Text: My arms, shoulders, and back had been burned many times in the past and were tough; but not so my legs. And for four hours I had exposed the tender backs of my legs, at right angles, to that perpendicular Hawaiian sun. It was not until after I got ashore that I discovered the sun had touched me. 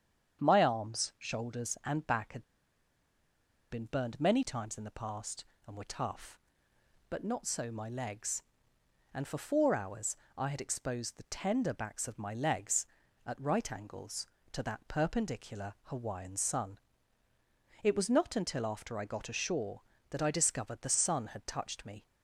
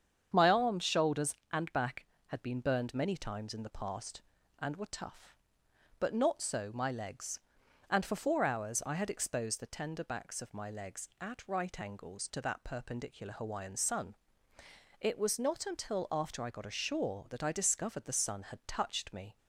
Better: second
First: starts louder than the rest; strong; until 1.4 s; 8 dB // pauses between "had" and "been"; strong; at 2.4 s; 1.2 s long // pauses between "hours" and "I"; slight; at 10.1 s; 0.22 s long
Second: starts louder than the rest; strong; until 1.3 s; 8 dB

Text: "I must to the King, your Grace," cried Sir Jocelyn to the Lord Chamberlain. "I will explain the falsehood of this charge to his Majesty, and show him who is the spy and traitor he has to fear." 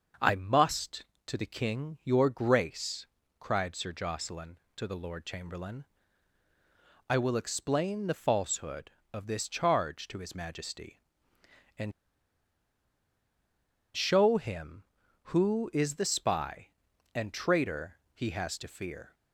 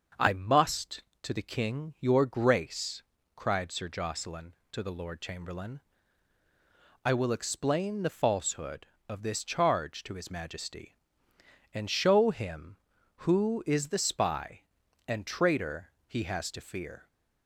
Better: second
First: starts louder than the rest; until 1.4 s; 6.5 dB // pauses between "and" and "show"; strong; at 11.9 s; 2.0 s long // pauses between "traitor" and "he"; slight; at 17.9 s; 0.16 s long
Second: starts louder than the rest; until 1.3 s; 6.5 dB // pauses between "traitor" and "he"; slight; at 15.9 s; 0.16 s long

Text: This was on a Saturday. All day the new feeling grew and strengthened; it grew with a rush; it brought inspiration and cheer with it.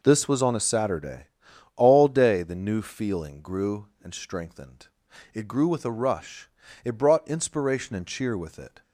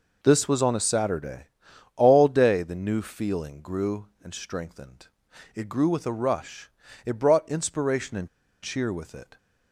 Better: first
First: none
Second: pauses between "and" and "cheer"; slight; at 8.2 s; 0.35 s long

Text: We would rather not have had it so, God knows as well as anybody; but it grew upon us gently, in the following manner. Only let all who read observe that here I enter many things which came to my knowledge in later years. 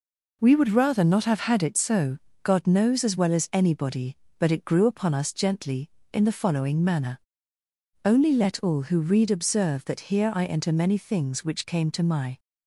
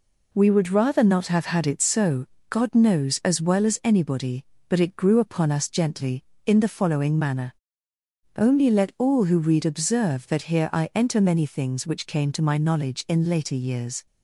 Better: second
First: stops before "knowledge in later years"; at 12.3 s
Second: none

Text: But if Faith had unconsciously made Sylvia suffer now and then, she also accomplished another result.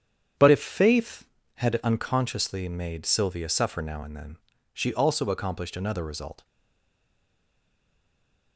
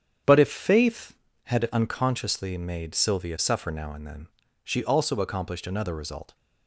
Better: second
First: starts louder than the rest; strong; until 1.6 s; 8.5 dB // stays silent after the last word; from 6.4 s on; 2.1 s long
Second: starts louder than the rest; strong; until 1.5 s; 8.5 dB

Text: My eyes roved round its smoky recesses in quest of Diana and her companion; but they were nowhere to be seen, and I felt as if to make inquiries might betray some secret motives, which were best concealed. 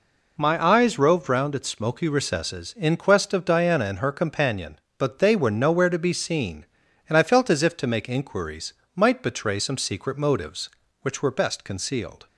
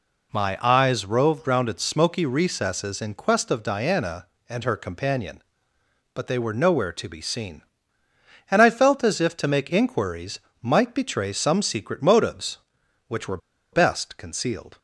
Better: first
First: pauses between "inquiries" and "might"; slight; at 8.7 s; 0.22 s long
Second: pauses between "inquiries" and "might"; slight; at 10.3 s; 0.24 s long // pauses between "were" and "best"; slight; at 13.3 s; 0.34 s long

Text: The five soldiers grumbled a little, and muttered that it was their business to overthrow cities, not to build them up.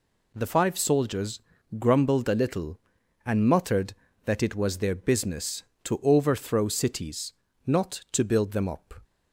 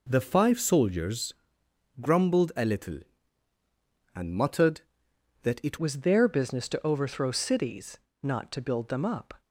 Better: first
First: pauses between "soldiers" and "grumbled"; at 1.3 s; 0.40 s long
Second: pauses between "soldiers" and "grumbled"; noticeable; at 1.3 s; 0.66 s long // changes voice at "was"; from 5.7 s on; 3.7 s long

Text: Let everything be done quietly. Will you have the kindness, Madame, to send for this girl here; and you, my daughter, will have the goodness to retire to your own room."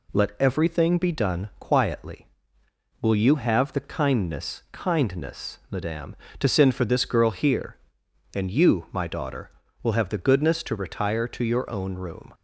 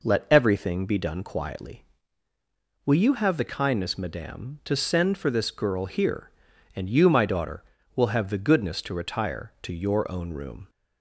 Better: second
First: says "kindness" twice; at 4.7 s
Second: none

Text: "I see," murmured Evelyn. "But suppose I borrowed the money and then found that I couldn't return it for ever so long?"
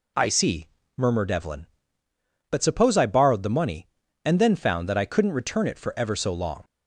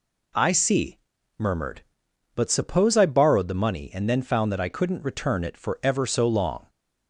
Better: first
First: none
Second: skips "Evelyn"; at 2.0 s

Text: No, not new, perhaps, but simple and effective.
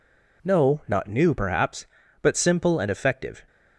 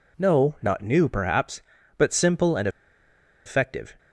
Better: first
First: none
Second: pauses between "and" and "effective"; noticeable; at 2.6 s; 0.77 s long

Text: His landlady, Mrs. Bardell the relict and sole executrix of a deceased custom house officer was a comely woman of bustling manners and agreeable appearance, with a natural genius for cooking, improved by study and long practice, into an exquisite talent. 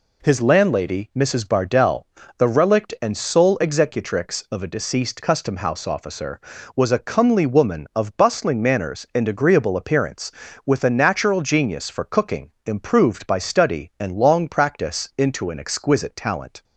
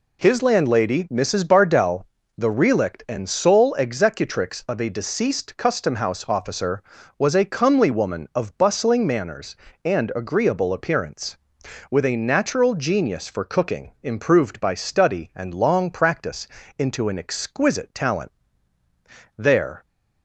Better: first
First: pauses between "Bardell" and "the"; slight; at 2.0 s; 0.32 s long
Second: pauses between "Bardell" and "the"; slight; at 2.0 s; 0.33 s long // goes on to say "There"; slight; from 19.3 s on; 0.48 s long

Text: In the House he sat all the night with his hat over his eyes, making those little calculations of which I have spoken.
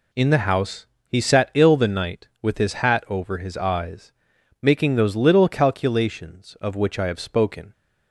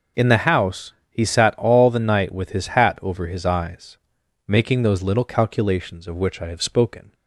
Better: second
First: pauses between "House" and "he"; slight; at 0.8 s; 0.22 s long // says "ill" for "all"; at 1.5 s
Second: pauses between "House" and "he"; slight; at 0.9 s; 0.18 s long

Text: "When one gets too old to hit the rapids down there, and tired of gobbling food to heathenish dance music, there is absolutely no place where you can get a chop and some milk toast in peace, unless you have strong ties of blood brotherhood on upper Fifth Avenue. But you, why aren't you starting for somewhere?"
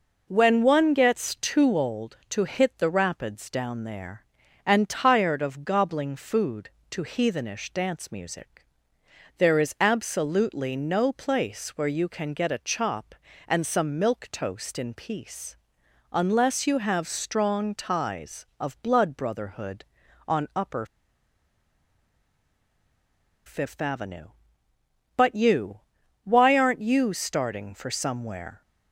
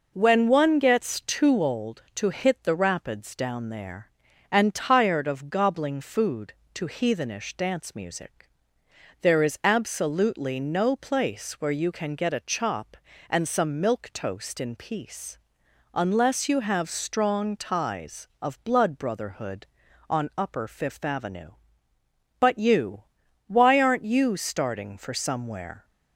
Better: second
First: pauses between "upper" and "Fifth"; strong; at 20.8 s; 2.6 s long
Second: none

